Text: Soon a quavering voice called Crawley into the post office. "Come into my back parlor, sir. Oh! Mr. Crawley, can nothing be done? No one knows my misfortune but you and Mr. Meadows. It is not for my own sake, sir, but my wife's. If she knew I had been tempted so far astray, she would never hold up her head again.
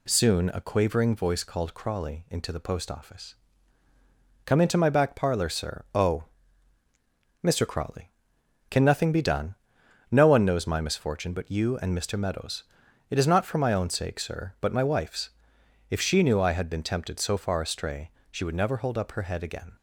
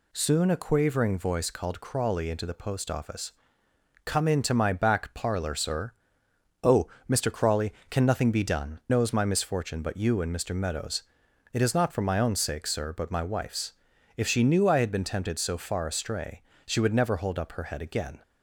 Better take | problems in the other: first | skips "No one"; at 8.8 s

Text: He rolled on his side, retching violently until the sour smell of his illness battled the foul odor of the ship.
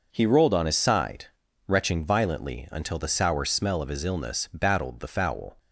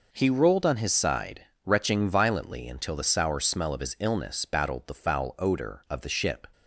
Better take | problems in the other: second | stops before "odor of the ship"; at 5.5 s

